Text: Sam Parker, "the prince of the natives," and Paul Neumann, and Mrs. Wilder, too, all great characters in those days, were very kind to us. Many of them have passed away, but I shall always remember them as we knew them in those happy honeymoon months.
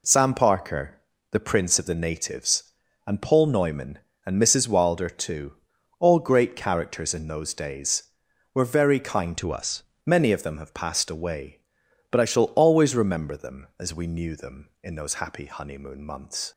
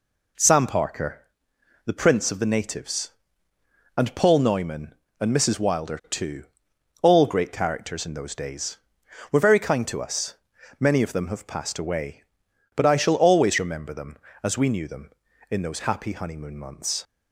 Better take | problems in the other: second | changes voice from "to" to "us"; from 9.3 to 9.8 s; 0.5 s long

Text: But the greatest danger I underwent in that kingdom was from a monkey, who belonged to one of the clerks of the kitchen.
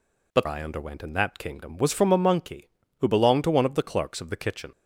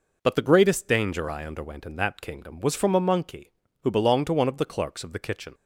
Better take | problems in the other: second | skips "the greatest danger"; at 0.4 s

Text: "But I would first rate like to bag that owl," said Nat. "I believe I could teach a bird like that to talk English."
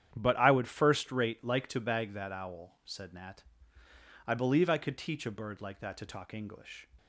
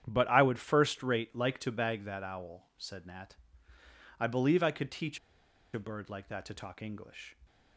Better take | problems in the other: first | starts louder than the rest; strong; until 1.0 s; 9.5 dB; strong in the first // pauses between "teach" and "a"; noticeable; at 5.1 s; 0.56 s long

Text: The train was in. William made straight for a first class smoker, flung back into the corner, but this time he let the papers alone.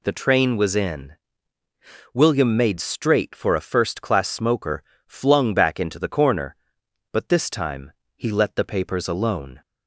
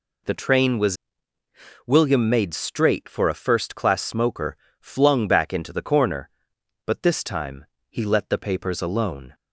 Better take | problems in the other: first | skips "in"; at 1.4 s // pauses between "time" and "he"; slight; at 7.6 s; 0.26 s long; slight in the first

